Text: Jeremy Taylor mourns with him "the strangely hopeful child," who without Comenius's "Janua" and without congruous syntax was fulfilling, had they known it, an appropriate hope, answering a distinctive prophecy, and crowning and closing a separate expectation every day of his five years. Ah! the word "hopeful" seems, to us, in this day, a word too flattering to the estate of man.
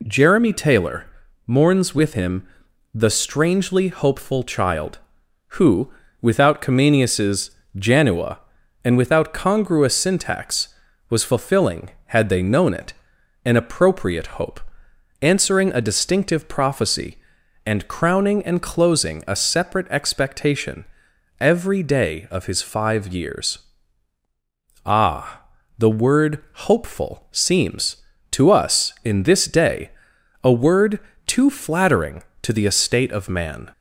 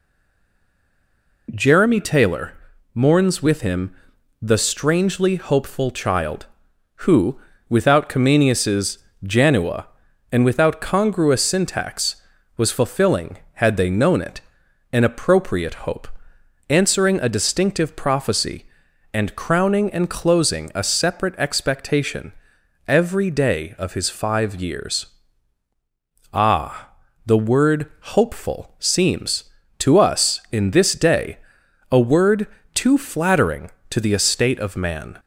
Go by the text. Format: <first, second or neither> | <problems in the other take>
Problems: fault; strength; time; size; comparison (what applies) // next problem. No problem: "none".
first | stays silent before the first word; noticeable; until 1.4 s; 1.4 s long // pauses between "Taylor" and "mourns"; at 2.5 s; 0.40 s long; also in the first // pauses between "him" and "the"; noticeable; at 3.9 s; 0.48 s long; noticeable in the first // pauses between "who" and "without"; slight; at 7.3 s; 0.28 s long; slight in the first // pauses between "Comenius's" and "Janua"; slight; at 8.9 s; 0.26 s long; slight in the first // pauses between "expectation" and "every"; noticeable; at 22.3 s; 0.54 s long; noticeable in the first // pauses between "word" and "hopeful"; slight; at 27.8 s; 0.28 s long; slight in the first // pauses between "word" and "too"; slight; at 32.4 s; 0.26 s long; slight in the first